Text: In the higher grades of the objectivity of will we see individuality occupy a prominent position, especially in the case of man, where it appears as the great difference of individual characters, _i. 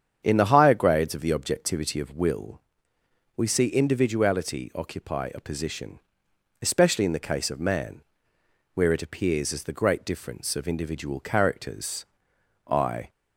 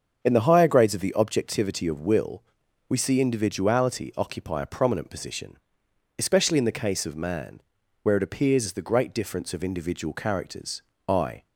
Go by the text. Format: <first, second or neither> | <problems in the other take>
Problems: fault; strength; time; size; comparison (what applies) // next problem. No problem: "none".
second | starts louder than the rest; strong; until 1.2 s; 8 dB; also in the second // pauses between "will" and "we"; noticeable; at 2.6 s; 0.74 s long; noticeable in the second // skips "prominent"; at 5.4 s